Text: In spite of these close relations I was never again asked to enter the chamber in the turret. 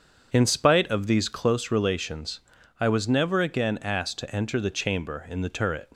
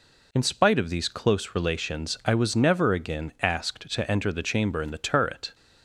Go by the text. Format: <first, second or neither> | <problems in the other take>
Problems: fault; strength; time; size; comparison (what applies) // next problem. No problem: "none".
second | starts louder than the rest; strong; until 1.3 s; 7.5 dB // pauses between "relations" and "I"; at 2.4 s; 0.40 s long